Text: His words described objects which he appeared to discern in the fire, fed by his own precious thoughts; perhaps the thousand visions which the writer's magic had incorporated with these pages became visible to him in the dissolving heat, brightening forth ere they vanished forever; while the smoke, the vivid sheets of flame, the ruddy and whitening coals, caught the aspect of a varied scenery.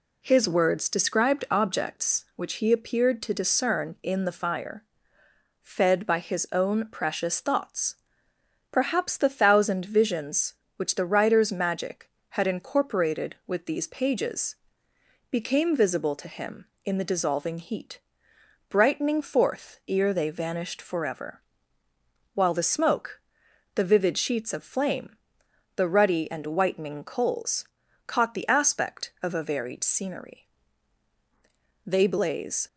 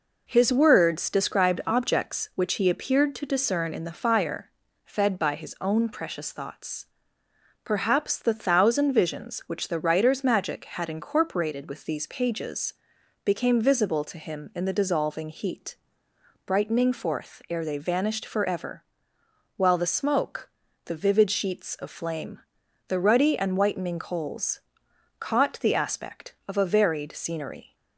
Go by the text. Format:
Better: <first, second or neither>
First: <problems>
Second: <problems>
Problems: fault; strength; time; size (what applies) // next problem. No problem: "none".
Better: second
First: pauses between "pages" and "became"; noticeable; at 14.5 s; 0.74 s long // goes on to say "They blaze"; noticeable; from 31.8 s on; 0.80 s long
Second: pauses between "pages" and "became"; noticeable; at 12.7 s; 0.50 s long